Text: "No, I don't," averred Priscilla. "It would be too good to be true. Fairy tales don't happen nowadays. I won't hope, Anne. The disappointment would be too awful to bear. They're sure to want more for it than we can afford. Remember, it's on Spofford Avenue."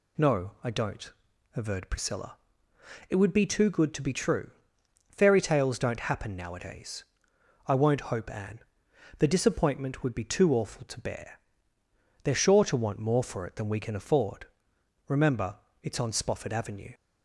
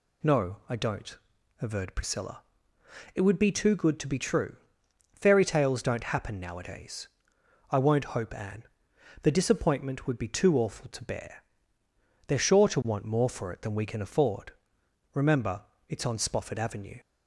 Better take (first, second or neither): neither